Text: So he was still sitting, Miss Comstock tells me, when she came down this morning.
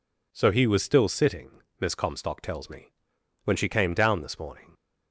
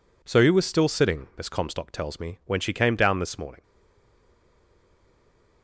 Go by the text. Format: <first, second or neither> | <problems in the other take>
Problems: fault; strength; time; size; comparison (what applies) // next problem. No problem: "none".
first | stays silent after the last word; noticeable; from 3.6 s on; 2.0 s long